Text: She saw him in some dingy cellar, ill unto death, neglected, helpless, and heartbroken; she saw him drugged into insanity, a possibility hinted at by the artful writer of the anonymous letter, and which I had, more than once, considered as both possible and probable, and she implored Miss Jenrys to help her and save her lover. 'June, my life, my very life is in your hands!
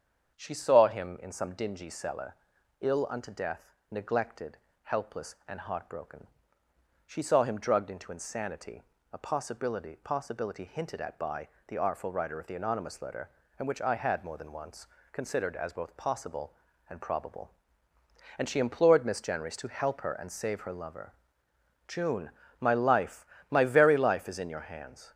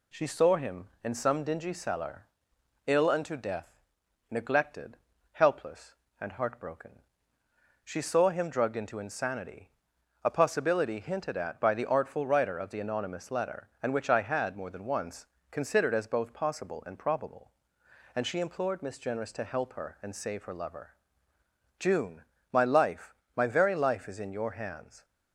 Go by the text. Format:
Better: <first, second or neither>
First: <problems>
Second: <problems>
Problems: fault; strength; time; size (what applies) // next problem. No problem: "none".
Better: second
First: starts louder than the rest; strong; until 1.4 s; 7.5 dB // says "possibility" twice; at 9.9 s // pauses between "by" and "the"; slight; at 11.4 s; 0.18 s long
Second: none